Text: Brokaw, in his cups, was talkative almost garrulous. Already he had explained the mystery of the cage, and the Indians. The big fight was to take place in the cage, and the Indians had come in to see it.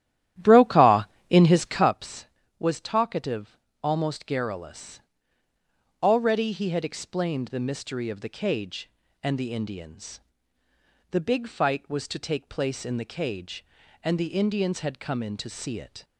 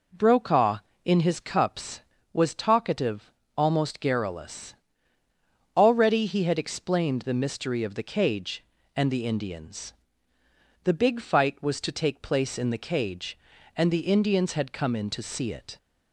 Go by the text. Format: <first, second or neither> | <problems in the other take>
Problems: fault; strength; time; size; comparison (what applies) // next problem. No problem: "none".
second | starts louder than the rest; strong; until 2.0 s; 12 dB // pauses between "talkative" and "almost"; slight; at 3.5 s; 0.26 s long; slight in the second